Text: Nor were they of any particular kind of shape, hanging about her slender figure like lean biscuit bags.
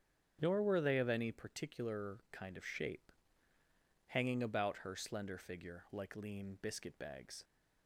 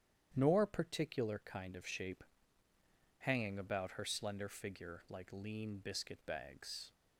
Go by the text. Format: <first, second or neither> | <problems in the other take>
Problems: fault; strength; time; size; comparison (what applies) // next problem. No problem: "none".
first | starts louder than the rest; strong; until 1.3 s; 10 dB; strong in the first // skips "were they of any"; at 0.6 s